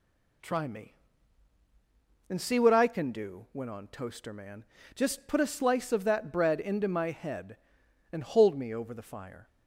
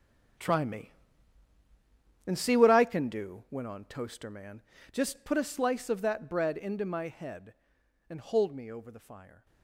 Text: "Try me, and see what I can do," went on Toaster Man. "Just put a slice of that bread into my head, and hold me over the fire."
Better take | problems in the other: first | gets quieter; strong; throughout; 12.5 dB

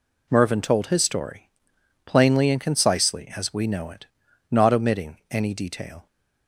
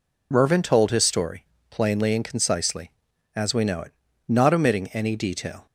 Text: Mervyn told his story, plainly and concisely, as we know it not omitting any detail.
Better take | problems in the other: neither | pauses between "it" and "not"; the same in both

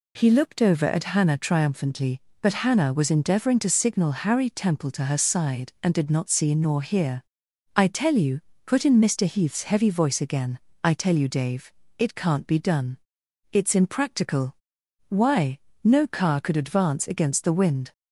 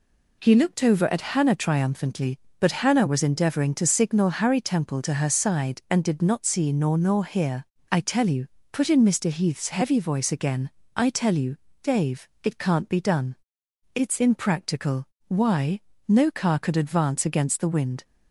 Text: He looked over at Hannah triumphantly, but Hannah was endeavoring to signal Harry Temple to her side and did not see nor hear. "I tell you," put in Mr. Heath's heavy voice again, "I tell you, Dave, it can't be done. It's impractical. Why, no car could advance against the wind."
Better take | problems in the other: first | says "nor" twice; at 6.9 s

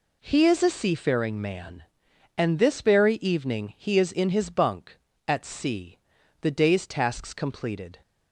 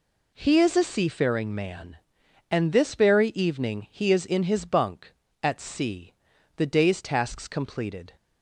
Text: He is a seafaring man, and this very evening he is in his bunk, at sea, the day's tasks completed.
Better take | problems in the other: neither | none

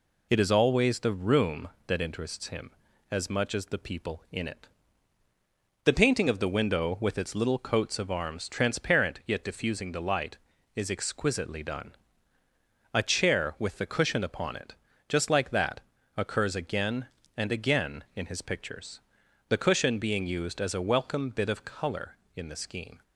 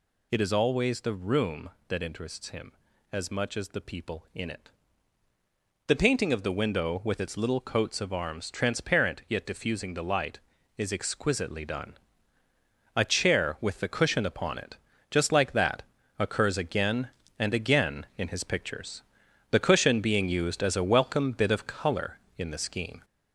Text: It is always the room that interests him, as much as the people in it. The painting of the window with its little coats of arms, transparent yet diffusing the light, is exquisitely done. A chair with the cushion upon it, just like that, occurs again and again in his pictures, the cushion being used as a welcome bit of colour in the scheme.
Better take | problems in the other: first | gets louder; noticeable; throughout; 4 dB

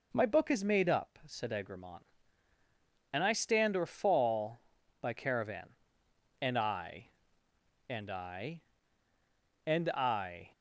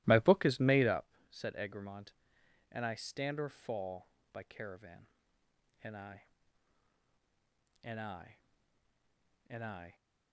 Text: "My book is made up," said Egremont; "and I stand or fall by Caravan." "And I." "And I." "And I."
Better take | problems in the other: first | starts louder than the rest; strong; until 1.1 s; 17 dB

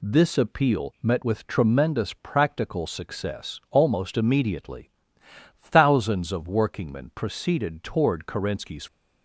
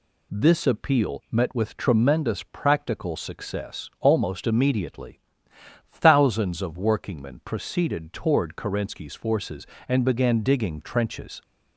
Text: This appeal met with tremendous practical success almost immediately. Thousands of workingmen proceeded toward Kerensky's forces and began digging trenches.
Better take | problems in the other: second | stops before "forces and began digging trenches"; at 8.8 s

